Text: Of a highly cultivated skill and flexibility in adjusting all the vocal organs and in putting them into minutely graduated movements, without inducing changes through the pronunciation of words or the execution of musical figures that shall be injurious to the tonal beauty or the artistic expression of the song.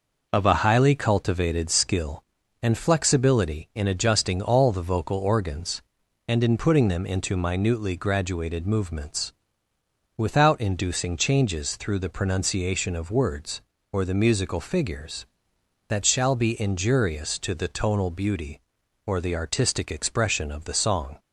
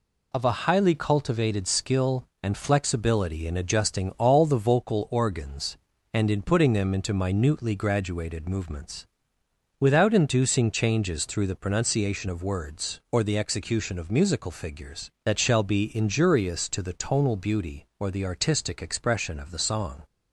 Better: second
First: skips "execution of"; at 14.2 s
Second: none

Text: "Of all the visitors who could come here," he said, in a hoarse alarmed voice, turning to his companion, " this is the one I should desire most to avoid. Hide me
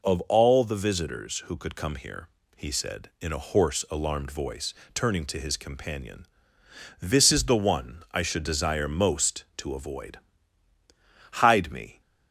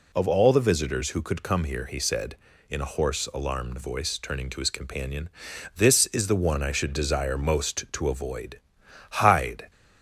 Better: first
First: none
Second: stops before "me"; at 9.7 s

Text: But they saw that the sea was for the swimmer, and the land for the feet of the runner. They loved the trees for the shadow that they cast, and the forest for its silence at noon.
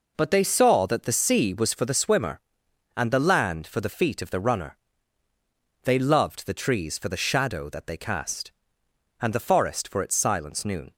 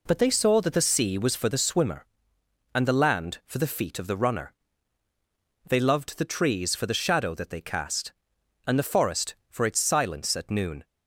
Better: second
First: skips "at"; at 10.6 s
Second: none

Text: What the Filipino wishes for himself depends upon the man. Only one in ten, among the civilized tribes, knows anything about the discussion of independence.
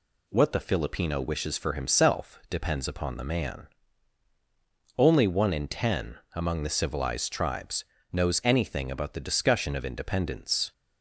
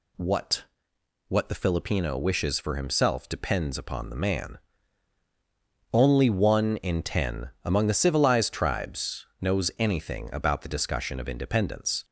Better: first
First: none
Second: says "What" twice; at 1.2 s

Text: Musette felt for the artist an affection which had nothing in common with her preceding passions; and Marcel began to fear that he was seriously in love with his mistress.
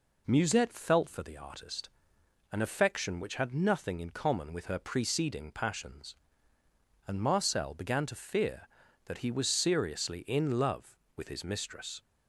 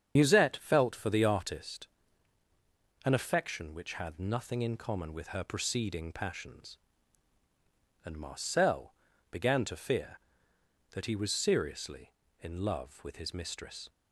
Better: first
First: pauses between "artist" and "an"; noticeable; at 1.9 s; 0.60 s long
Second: loses the start of "Musette"; at 0.1 s; 70 ms // starts louder than the rest; strong; until 1.1 s; 7.5 dB // pauses between "artist" and "an"; at 1.8 s; 1.1 s long // pauses between "Marcel" and "began"; slight; at 8.9 s; 0.34 s long

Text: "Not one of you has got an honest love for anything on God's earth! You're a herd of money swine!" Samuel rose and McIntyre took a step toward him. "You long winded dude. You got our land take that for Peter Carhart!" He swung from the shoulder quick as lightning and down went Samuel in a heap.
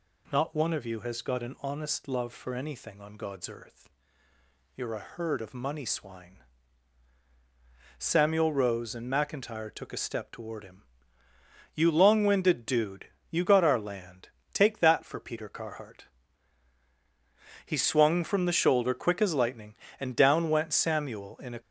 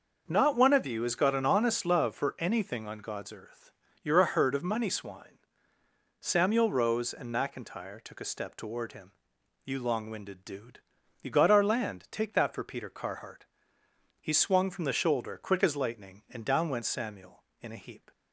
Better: second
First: pauses between "land" and "take"; slight; at 14.3 s; 0.22 s long // stops before "heap"; at 21.6 s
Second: none

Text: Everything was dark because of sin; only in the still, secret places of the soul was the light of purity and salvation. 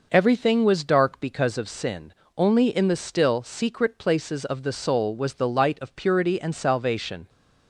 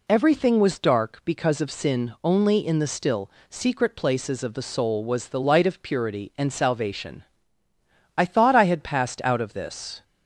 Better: first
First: none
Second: goes on to say "I thought I had passed out of this"; strong; from 8.1 s on; 1.8 s long

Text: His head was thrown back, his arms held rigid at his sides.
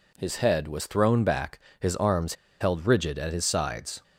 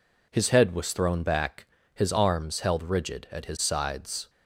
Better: second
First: pauses between "arms" and "held"; slight; at 2.3 s; 0.26 s long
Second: none

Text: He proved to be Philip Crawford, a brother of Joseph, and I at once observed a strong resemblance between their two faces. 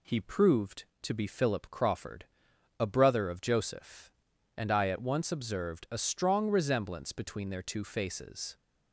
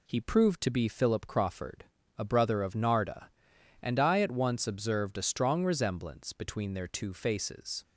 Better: first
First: none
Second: says "Narda" for "Joseph"; at 2.7 s

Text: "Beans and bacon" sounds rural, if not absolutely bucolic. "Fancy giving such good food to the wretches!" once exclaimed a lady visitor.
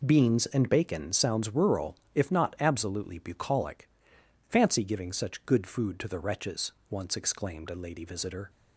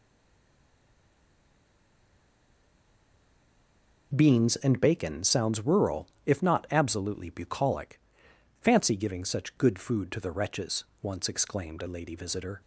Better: first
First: none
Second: stays silent before the first word; strong; until 4.1 s; 4.1 s long

